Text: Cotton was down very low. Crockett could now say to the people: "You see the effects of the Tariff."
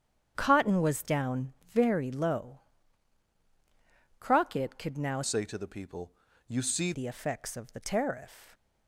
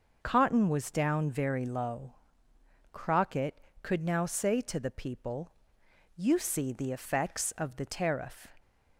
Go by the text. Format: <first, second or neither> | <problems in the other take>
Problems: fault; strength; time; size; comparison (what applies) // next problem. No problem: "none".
second | starts louder than the rest; strong; until 1.3 s; 8.5 dB // pauses between "down" and "very"; slight; at 1.5 s; 0.16 s long // changes voice from "say" to "see"; from 5.2 to 6.9 s; 1.7 s long